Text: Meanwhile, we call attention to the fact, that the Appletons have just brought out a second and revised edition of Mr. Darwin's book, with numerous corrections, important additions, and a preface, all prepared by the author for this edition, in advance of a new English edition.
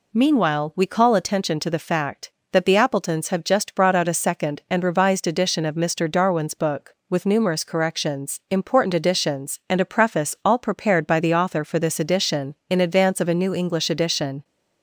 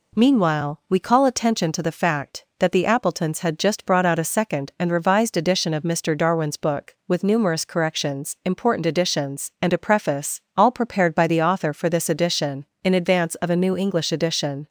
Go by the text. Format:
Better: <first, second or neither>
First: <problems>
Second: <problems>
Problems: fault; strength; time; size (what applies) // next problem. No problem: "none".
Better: first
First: none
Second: says "had" for "have"; at 3.3 s